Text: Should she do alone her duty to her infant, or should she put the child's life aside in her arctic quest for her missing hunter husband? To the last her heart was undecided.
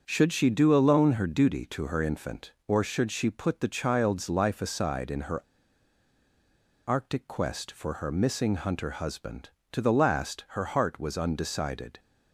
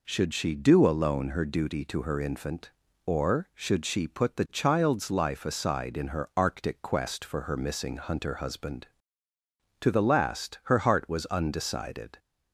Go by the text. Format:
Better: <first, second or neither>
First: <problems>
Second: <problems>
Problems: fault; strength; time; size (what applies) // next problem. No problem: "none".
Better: second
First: starts louder than the rest; until 1.0 s; 6.5 dB // pauses between "her" and "arctic"; strong; at 5.4 s; 1.4 s long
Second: none